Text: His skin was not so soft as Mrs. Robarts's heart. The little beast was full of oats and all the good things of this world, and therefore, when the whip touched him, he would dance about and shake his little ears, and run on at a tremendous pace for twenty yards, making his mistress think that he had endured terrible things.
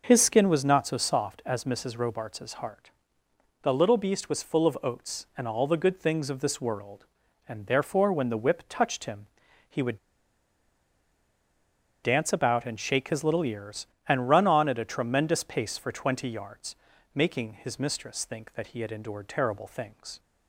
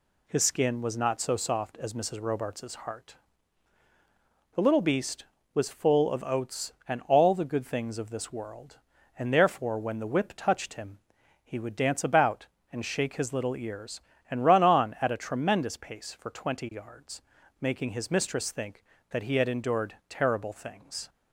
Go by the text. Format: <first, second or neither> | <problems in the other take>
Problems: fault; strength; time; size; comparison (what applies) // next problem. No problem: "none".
second | pauses between "would" and "dance"; strong; at 9.9 s; 2.0 s long